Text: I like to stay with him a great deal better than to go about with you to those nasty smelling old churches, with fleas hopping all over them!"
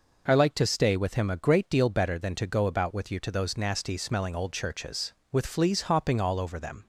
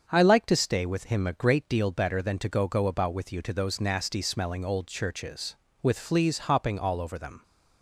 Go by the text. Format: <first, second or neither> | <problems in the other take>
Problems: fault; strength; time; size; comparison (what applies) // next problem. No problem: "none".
first | starts louder than the rest; until 1.0 s; 7 dB // says "go" twice; at 2.6 s